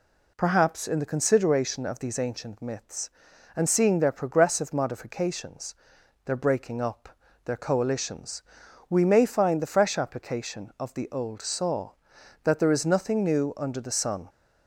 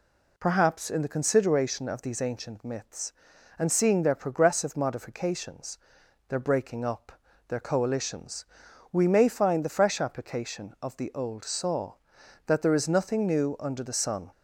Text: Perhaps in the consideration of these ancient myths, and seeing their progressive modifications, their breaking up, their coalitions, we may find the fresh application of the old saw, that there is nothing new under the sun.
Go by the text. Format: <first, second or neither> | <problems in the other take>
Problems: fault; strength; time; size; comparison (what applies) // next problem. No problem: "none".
neither | none